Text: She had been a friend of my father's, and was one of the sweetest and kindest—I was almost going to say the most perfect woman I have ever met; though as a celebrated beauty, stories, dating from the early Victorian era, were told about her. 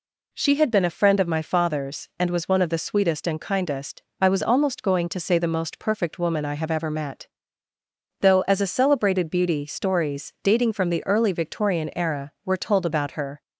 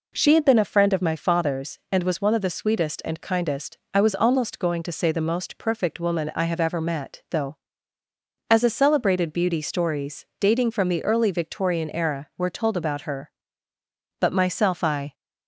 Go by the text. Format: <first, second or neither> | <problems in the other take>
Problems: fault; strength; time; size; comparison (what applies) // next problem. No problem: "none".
first | goes on to say "But myself I"; noticeable; from 14.1 s on; 0.94 s long